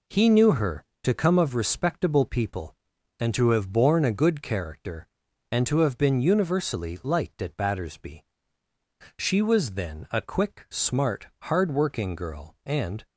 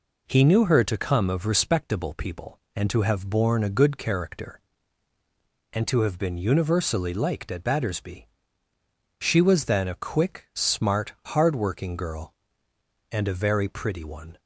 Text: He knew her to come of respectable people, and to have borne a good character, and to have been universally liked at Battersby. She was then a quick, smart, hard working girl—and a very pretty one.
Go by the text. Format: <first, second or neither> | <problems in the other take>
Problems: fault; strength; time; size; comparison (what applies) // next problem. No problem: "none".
second | stops before "a very pretty one"; at 13.0 s